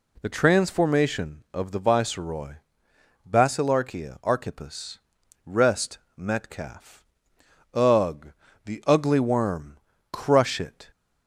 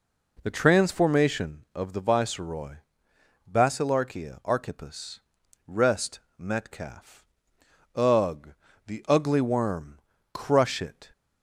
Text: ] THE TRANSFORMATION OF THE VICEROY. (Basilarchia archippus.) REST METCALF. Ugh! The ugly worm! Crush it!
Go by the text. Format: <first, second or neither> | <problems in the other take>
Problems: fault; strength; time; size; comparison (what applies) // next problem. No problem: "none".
first | starts louder than the rest; noticeable; until 1.6 s; 4 dB // pauses between "REST" and "METCALF"; slight; at 6.1 s; 0.18 s long; slight in the first